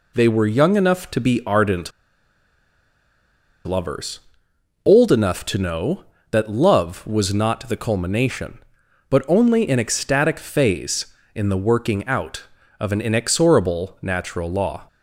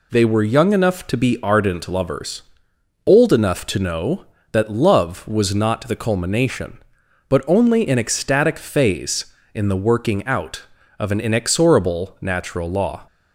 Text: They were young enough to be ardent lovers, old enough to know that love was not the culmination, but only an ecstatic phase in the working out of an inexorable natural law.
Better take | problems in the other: second | pauses between "ardent" and "lovers"; strong; at 1.9 s; 1.7 s long

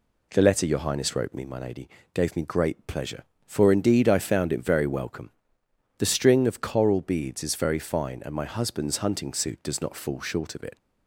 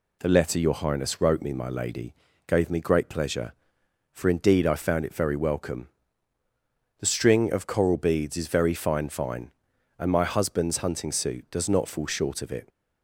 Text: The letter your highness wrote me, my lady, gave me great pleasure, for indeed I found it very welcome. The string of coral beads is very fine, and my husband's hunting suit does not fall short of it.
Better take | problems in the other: first | says "fine" twice; at 9.0 s

